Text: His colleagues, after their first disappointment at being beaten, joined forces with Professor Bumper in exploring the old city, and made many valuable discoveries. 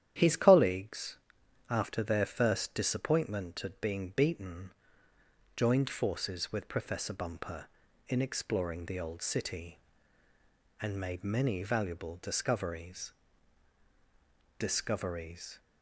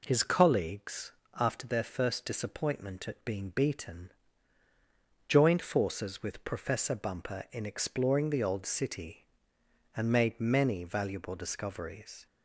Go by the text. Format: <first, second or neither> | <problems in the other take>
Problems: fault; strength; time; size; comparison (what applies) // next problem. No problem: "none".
second | starts louder than the rest; strong; until 1.1 s; 10.5 dB // says "discoveries" twice; at 14.5 s